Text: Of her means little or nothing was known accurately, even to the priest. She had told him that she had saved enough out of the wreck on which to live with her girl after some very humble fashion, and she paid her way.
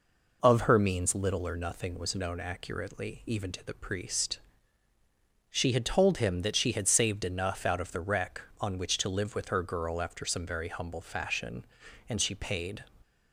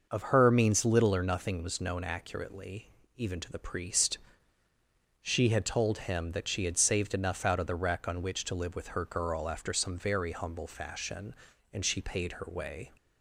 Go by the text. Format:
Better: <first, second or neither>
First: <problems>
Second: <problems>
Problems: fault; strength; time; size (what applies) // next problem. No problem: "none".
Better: second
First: stops before "her way"; at 13.0 s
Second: none